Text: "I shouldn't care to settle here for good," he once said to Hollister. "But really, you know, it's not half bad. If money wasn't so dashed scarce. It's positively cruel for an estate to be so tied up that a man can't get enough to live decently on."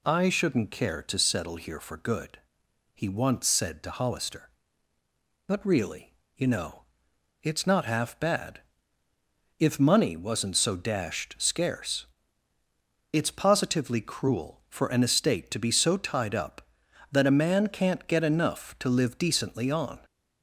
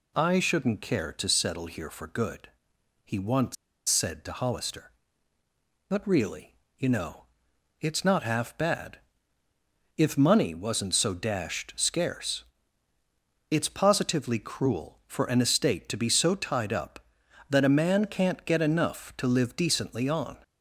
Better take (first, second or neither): first